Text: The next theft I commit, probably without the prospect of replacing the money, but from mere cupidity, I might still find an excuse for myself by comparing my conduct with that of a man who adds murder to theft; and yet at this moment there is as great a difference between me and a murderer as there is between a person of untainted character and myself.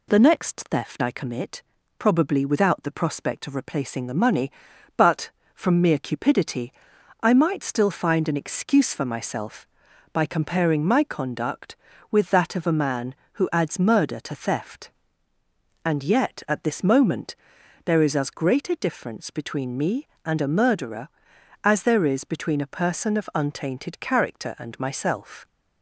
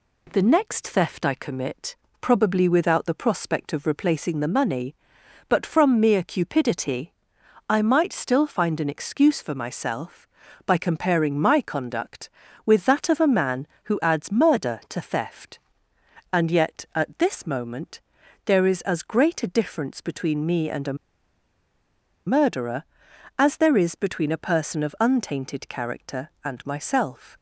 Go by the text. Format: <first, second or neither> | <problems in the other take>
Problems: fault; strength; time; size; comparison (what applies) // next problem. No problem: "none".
first | pauses between "moment" and "there"; at 18.0 s; 0.42 s long; noticeable in the first // pauses between "a" and "murderer"; strong; at 20.9 s; 1.3 s long